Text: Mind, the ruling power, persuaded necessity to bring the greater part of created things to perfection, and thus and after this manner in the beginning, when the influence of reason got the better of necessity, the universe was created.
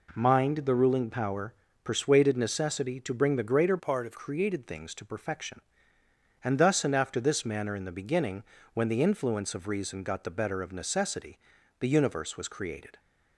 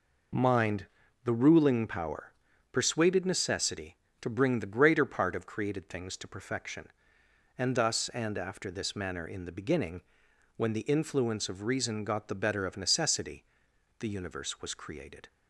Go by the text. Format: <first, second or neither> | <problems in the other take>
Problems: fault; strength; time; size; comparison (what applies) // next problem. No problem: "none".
second | changes voice from "part" to "of"; from 3.7 to 4.1 s; 0.4 s long